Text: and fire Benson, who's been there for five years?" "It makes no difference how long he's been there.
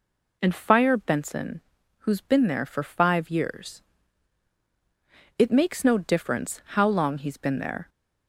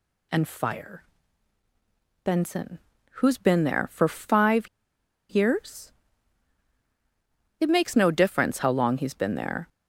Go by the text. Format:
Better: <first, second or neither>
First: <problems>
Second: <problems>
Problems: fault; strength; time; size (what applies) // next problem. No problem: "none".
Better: first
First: none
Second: pauses between "fire" and "Benson"; at 1.0 s; 1.2 s long // pauses between "five" and "years"; noticeable; at 4.6 s; 0.62 s long